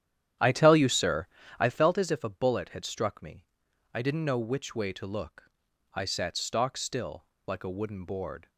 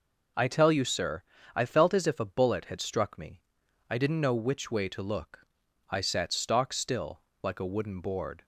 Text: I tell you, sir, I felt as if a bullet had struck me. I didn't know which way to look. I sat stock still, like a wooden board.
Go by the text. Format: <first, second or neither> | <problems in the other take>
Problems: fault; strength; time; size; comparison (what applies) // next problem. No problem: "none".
second | starts louder than the rest; strong; until 1.8 s; 10.5 dB